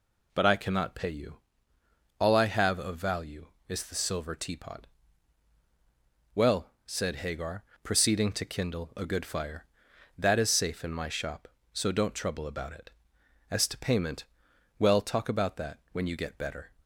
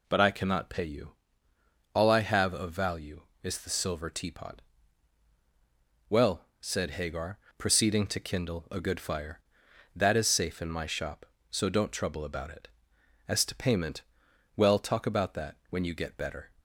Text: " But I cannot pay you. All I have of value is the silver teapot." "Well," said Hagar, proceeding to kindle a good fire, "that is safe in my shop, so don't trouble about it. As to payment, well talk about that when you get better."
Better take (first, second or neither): neither